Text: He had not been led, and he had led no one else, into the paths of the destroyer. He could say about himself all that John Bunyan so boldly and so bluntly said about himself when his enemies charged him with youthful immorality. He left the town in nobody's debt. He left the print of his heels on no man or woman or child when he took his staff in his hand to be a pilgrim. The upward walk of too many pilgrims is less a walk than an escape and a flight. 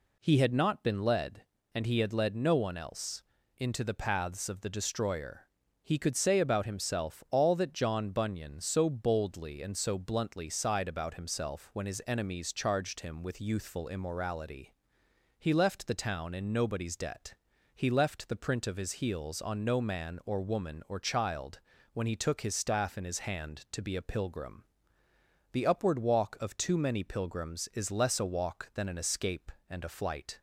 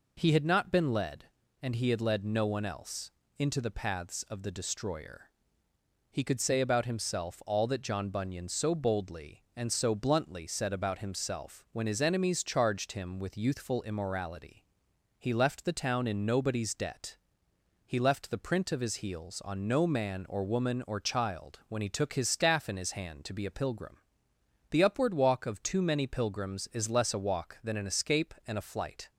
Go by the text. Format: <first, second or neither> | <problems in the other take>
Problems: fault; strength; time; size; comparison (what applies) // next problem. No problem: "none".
second | says "sighed" for "said"; at 10.4 s // pauses between "child" and "when"; slight; at 21.6 s; 0.32 s long